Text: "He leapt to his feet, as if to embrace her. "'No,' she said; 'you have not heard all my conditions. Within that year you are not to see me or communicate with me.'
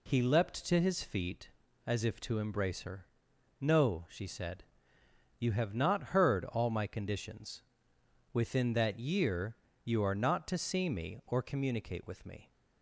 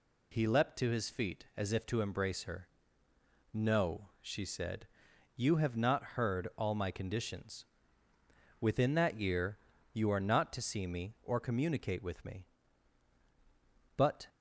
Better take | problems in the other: first | pauses between "year" and "you"; slight; at 9.5 s; 0.34 s long; slight in the first // goes on to say "But"; slight; from 13.9 s on; 0.30 s long

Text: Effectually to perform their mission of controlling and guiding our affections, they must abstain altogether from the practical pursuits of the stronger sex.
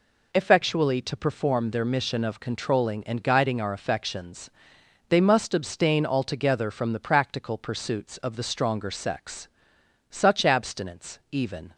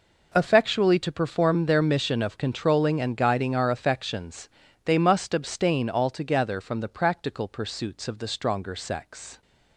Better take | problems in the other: second | goes on to say "Such abstinence even"; from 10.1 s on; 1.6 s long

